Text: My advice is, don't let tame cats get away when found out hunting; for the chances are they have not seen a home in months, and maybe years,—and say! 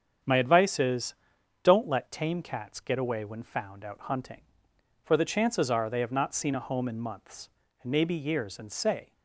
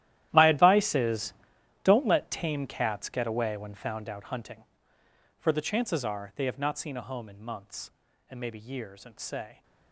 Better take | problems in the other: first | gets quieter; strong; throughout; 16.5 dB // starts louder than the rest; strong; until 1.3 s; 13 dB; strong in the first

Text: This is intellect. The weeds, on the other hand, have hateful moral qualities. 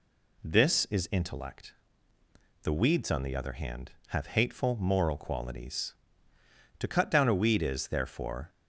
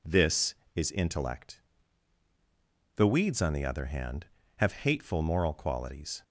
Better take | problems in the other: second | goes on to say "To cut down a weed is therefore"; strong; from 6.7 s on; 1.7 s long

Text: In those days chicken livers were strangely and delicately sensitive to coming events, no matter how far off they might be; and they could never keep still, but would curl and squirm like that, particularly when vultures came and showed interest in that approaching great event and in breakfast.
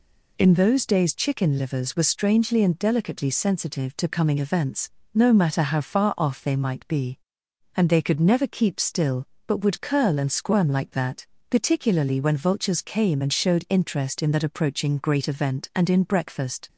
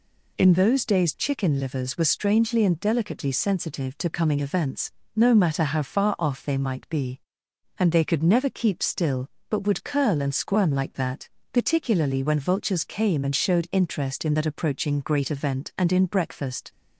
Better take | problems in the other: neither | none

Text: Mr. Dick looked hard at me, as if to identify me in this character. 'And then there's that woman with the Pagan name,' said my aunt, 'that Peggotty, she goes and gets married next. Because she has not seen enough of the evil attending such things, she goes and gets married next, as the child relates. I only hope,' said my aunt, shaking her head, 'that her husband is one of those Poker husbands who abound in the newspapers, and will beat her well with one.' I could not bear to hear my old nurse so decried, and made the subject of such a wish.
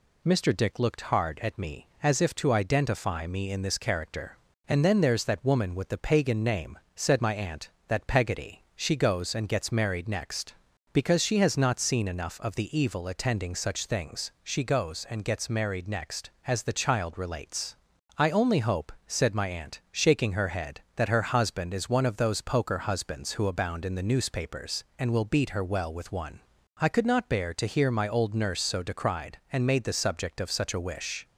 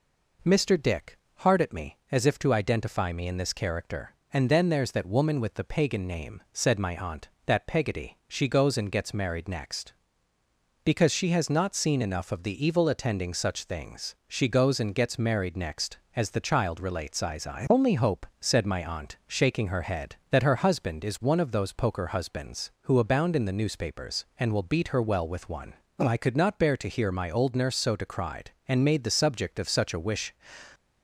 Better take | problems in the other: first | skips "looked"; at 1.2 s

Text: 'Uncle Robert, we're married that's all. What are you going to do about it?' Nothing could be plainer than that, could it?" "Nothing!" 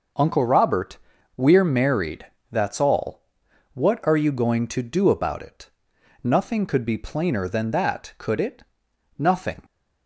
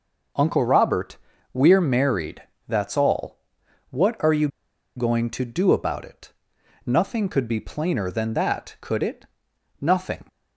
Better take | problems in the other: first | pauses between "married" and "that's"; slight; at 2.4 s; 0.22 s long; slight in the first // pauses between "you" and "going"; noticeable; at 4.4 s; 0.49 s long

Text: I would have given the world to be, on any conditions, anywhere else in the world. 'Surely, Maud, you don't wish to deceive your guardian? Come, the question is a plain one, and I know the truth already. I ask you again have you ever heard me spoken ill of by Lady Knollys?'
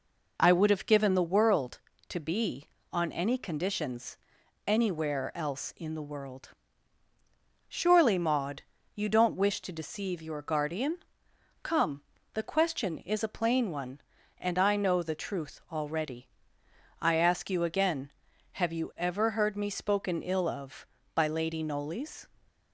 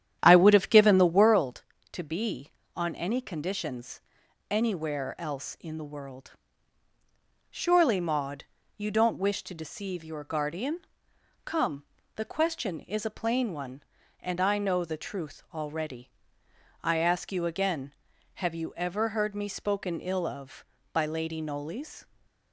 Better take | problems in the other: first | starts louder than the rest; strong; until 1.5 s; 10 dB // stays silent after the last word; slight; from 22.0 s on; 0.5 s long

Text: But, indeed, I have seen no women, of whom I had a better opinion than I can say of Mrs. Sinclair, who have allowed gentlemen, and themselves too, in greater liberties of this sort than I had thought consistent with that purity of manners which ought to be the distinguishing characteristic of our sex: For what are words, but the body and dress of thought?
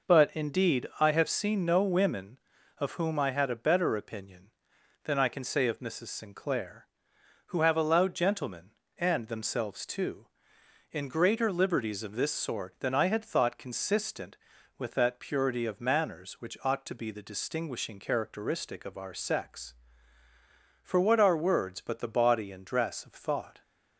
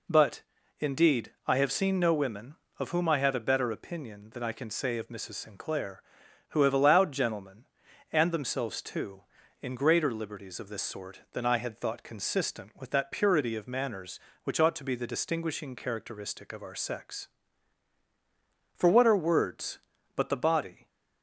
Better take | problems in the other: first | stops before "and dress of thought"; at 20.8 s

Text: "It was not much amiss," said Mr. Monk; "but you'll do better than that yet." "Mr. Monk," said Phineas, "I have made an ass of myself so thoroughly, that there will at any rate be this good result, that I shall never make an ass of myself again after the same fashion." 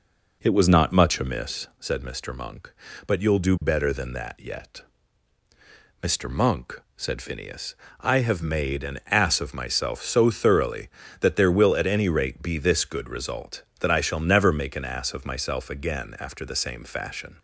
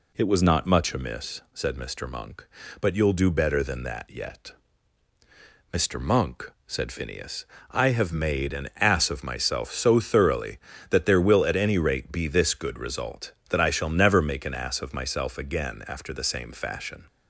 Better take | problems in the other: second | starts louder than the rest; noticeable; until 2.0 s; 4 dB

